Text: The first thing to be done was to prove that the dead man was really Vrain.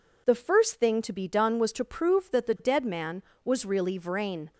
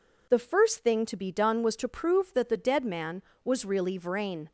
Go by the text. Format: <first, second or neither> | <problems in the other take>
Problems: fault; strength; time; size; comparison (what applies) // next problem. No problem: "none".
neither | none